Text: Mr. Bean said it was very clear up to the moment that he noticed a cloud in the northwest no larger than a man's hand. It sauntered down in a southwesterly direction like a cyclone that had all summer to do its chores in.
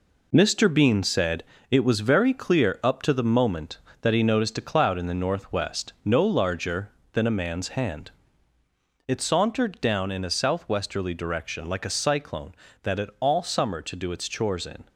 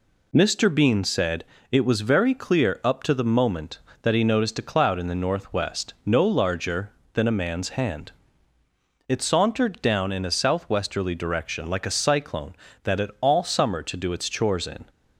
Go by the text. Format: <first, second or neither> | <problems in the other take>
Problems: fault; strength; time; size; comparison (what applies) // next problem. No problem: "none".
second | gets quieter; strong; throughout; 7 dB // pauses between "said" and "it"; slight; at 1.4 s; 0.28 s long; slight in the second